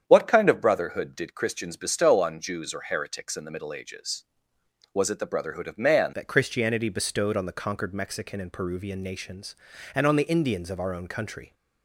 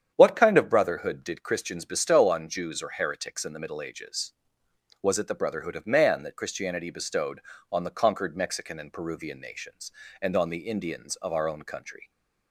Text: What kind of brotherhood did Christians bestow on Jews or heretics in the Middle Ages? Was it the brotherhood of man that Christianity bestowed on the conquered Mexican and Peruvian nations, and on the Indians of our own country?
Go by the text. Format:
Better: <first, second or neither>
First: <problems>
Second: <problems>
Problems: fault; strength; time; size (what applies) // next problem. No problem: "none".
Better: second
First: starts louder than the rest; strong; until 1.0 s; 8.5 dB // changes voice at "that"; from 6.1 s on; 5.4 s long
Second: starts louder than the rest; strong; until 1.1 s; 8.5 dB